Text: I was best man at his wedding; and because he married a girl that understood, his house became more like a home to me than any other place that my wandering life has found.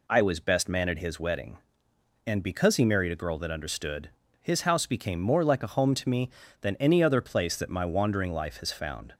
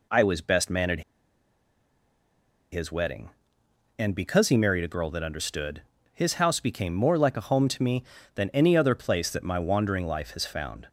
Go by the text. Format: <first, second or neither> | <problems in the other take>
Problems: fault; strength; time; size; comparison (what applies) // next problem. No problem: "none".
first | pauses between "at" and "his"; strong; at 1.0 s; 1.7 s long